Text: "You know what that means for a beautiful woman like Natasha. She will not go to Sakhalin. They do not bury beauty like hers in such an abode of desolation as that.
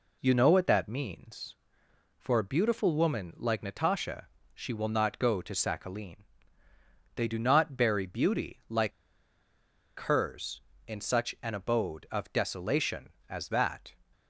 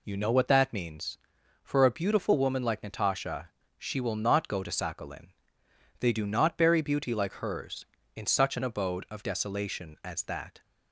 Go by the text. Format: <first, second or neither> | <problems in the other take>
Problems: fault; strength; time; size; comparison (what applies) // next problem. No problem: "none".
second | pauses between "like" and "hers"; at 8.9 s; 1.0 s long